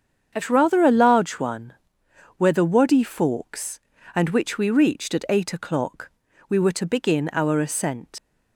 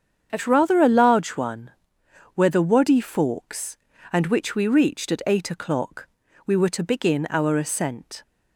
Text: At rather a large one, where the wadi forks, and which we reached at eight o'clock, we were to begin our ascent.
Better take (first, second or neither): second